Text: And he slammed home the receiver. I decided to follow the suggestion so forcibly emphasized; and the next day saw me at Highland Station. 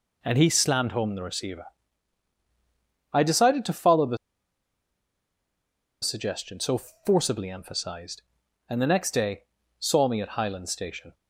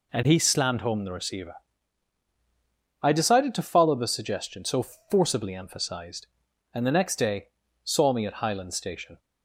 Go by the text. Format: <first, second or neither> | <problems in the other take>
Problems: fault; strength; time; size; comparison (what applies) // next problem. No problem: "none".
second | pauses between "the" and "suggestion"; strong; at 4.1 s; 1.8 s long // pauses between "so" and "forcibly"; slight; at 6.7 s; 0.26 s long; slight in the second // pauses between "day" and "saw"; slight; at 9.4 s; 0.36 s long; slight in the second